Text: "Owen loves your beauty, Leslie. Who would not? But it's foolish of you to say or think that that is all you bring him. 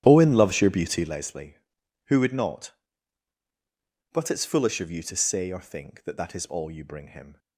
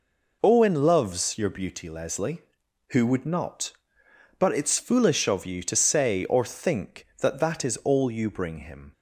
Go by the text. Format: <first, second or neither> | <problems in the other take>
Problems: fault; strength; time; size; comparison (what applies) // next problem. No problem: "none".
second | starts louder than the rest; strong; until 1.2 s; 11 dB